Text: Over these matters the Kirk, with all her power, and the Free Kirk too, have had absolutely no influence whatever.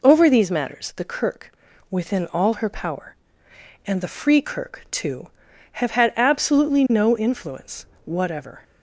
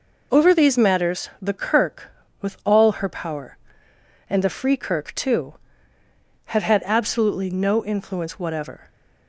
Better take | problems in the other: second | says "within" for "with"; at 1.9 s // pauses between "influence" and "whatever"; slight; at 7.8 s; 0.18 s long

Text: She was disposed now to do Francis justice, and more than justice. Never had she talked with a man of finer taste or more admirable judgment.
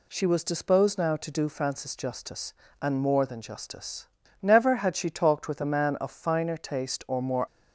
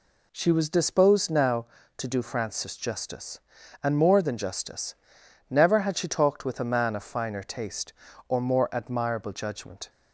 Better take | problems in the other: second | stops before "admirable judgment"; at 7.4 s

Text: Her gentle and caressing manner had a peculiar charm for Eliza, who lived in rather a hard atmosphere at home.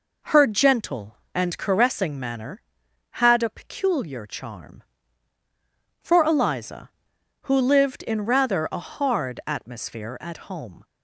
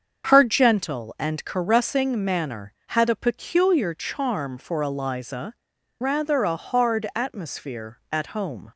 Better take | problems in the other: first | starts louder than the rest; until 1.3 s; 7 dB // skips "who lived in"; at 5.7 s

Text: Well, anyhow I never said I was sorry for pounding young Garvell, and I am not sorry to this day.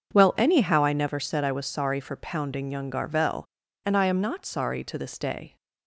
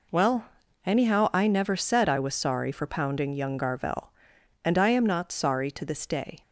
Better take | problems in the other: neither | none

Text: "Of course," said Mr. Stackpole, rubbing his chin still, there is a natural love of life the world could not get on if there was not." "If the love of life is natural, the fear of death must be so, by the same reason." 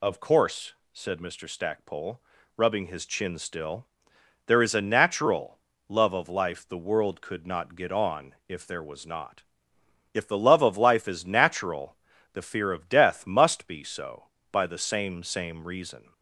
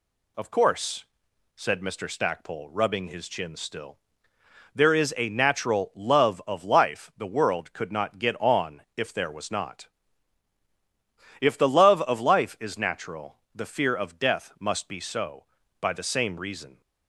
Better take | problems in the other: second | pauses between "natural" and "love"; slight; at 5.5 s; 0.30 s long // says "same" twice; at 15.2 s

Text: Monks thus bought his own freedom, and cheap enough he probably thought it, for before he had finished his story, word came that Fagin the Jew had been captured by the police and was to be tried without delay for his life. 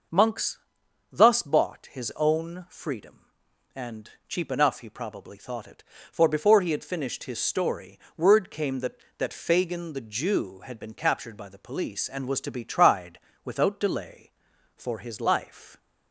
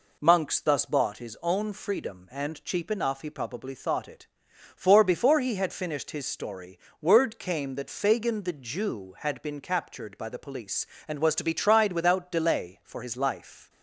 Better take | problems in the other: second | starts louder than the rest; noticeable; until 1.6 s; 6 dB // pauses between "Monks" and "thus"; noticeable; at 0.5 s; 0.54 s long // pauses between "and" and "cheap"; slight; at 4.0 s; 0.18 s long // says "that" twice; at 9.1 s // pauses between "tried" and "without"; slight; at 13.1 s; 0.24 s long

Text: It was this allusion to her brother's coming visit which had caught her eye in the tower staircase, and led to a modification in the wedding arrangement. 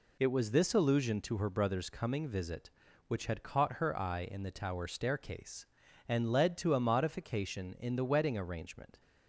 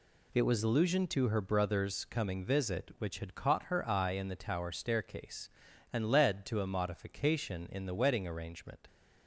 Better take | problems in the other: first | skips "this"; at 0.6 s

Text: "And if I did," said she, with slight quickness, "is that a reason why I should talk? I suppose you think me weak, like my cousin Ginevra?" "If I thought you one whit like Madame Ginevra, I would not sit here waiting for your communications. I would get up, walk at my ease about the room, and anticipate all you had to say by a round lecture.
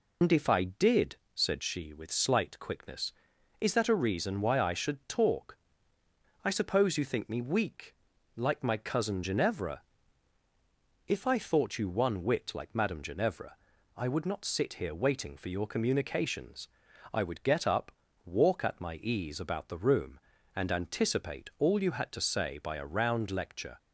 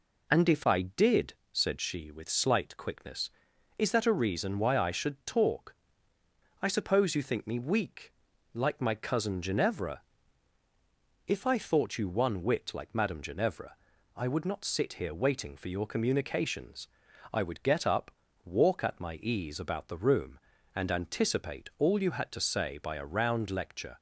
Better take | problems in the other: second | loses the start of "And"; at 0.2 s; 75 ms

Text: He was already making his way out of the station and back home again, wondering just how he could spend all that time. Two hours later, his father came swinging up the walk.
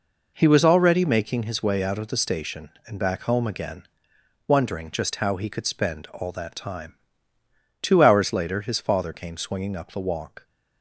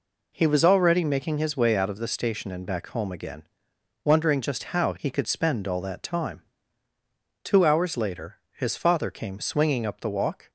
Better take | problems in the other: neither | none

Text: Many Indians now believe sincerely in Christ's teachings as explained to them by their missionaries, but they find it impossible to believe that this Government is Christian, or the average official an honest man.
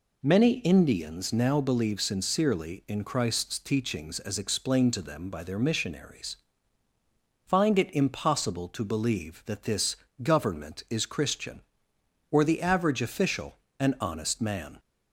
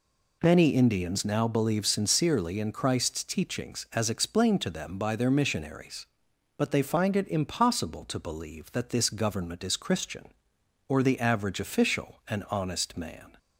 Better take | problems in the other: second | skips "but they"; at 6.9 s // pauses between "this" and "Government"; slight; at 9.9 s; 0.24 s long // pauses between "official" and "an"; slight; at 13.5 s; 0.20 s long

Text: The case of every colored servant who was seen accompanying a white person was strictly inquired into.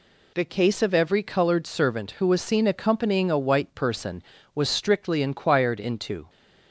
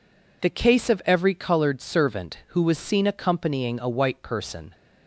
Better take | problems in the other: first | stops before "was strictly inquired into"; at 4.7 s

